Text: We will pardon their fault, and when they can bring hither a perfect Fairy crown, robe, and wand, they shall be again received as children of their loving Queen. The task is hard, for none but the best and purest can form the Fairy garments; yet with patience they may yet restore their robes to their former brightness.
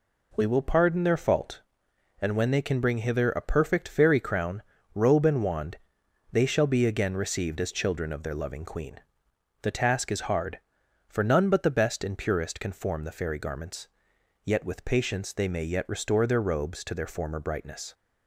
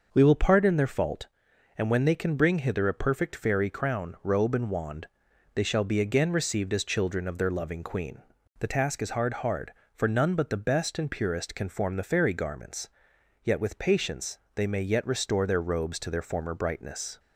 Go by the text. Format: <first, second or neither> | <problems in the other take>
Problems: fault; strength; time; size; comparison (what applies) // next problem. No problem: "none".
first | says "hard" twice; at 9.3 s // pauses between "patience" and "they"; slight; at 14.3 s; 0.18 s long